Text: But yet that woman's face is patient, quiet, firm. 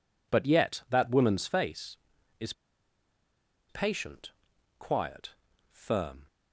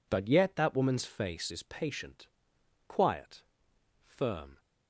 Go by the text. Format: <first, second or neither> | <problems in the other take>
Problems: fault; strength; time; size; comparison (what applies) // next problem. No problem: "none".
second | pauses between "is" and "patient"; at 2.5 s; 1.1 s long